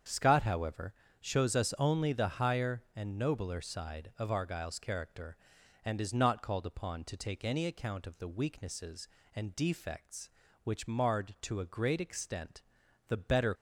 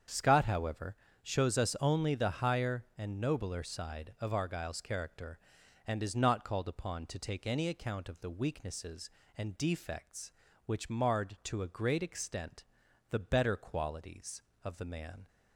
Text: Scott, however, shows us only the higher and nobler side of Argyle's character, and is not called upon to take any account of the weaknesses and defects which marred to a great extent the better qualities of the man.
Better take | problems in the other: second | starts louder than the rest; strong; until 1.3 s; 7.5 dB; strong in the second // pauses between "extent" and "the"; noticeable; at 12.6 s; 0.48 s long; noticeable in the second // stops before "qualities of the man"; at 13.5 s

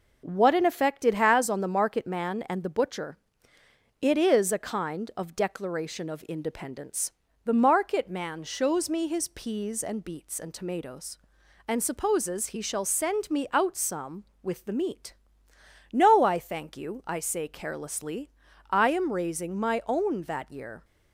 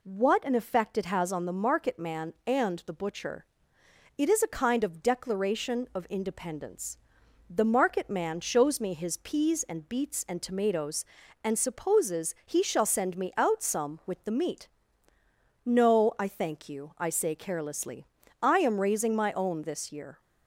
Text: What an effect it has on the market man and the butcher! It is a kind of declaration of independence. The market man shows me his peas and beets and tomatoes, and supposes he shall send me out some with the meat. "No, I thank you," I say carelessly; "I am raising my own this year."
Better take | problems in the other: second | says "that" for "this"; at 20.2 s

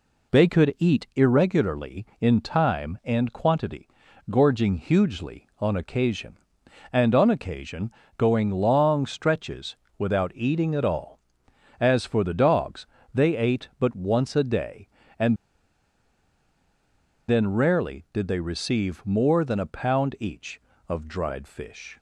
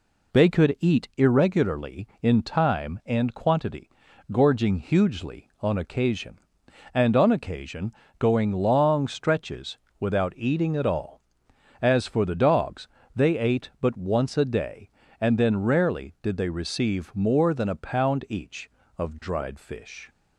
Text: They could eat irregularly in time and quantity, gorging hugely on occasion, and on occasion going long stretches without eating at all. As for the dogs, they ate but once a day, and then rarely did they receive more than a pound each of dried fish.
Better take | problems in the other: second | pauses between "occasion" and "going"; slight; at 7.9 s; 0.26 s long; slight in the second // pauses between "stretches" and "without"; slight; at 9.7 s; 0.22 s long; slight in the second // pauses between "and" and "then"; strong; at 15.3 s; 1.9 s long

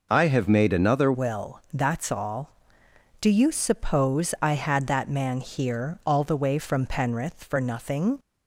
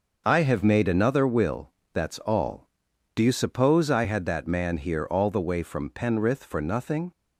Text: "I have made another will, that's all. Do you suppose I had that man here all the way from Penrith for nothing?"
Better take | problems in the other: second | changes voice at "will"; from 1.1 s on; 7.0 s long

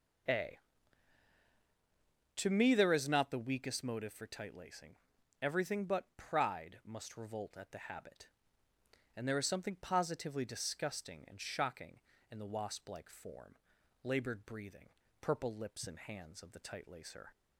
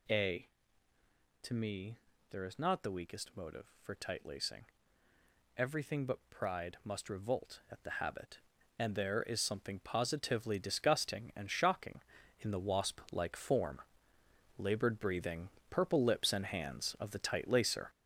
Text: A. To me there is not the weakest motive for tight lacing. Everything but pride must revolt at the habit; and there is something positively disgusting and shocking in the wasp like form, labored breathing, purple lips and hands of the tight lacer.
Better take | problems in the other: first | gets louder; noticeable; throughout; 6 dB // pauses between "me" and "there"; slight; at 1.9 s; 0.34 s long

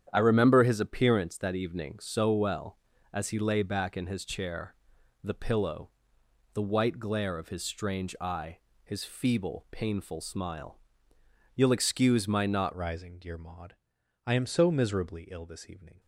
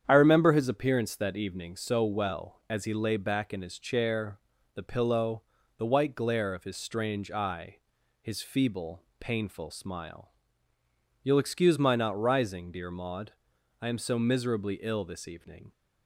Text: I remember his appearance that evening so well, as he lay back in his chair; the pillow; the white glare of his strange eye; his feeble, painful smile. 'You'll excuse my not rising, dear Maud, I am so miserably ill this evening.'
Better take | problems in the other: second | starts louder than the rest; strong; until 1.1 s; 9 dB; strong in the second // changes voice at "rising"; from 12.7 s on; 3.2 s long

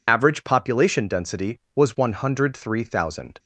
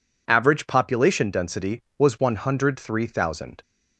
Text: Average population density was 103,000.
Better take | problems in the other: second | loses the start of "Average"; at 0.0 s; 30 ms

